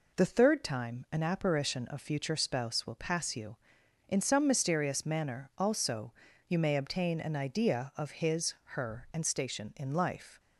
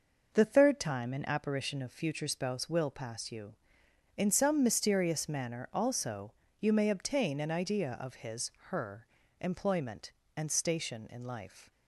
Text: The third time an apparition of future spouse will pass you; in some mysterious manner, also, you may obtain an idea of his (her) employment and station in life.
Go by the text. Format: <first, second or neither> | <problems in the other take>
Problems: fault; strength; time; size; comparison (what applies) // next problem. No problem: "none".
second | skips "employment"; at 9.1 s